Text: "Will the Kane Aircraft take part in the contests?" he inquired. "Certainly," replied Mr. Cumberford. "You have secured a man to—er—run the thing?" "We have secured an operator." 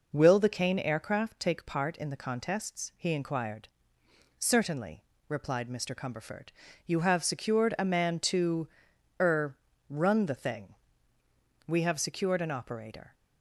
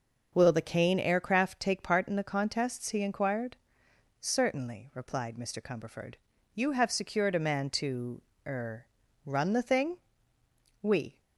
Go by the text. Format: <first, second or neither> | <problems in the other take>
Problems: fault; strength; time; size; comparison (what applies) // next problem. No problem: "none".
first | stops before "have secured an operator"; at 11.1 s